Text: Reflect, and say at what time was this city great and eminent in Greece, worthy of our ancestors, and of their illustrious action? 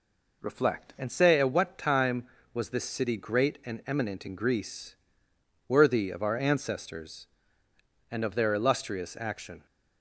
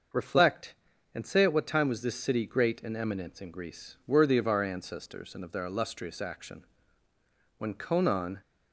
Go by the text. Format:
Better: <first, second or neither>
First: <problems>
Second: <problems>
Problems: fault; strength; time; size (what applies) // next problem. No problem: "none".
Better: first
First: none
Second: starts louder than the rest; until 1.5 s; 6 dB // goes on to say "when Conon"; noticeable; from 7.5 s on; 0.82 s long